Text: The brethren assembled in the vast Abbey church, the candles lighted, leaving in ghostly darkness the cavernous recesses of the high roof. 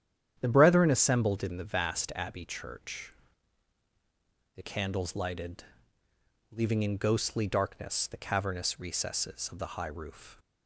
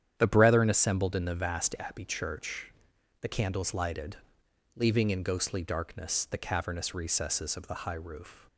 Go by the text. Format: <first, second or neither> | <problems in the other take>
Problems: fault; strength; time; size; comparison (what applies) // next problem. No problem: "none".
neither | starts louder than the rest; strong; the same in both